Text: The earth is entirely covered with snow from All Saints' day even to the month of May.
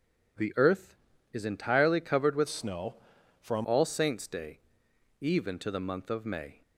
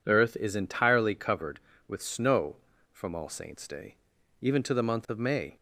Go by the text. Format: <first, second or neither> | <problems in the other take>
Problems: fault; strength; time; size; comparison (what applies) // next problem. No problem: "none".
second | changes voice from "snow" to "from"; from 2.4 to 3.6 s; 1.2 s long // pauses between "day" and "even"; noticeable; at 4.5 s; 0.62 s long; noticeable in the second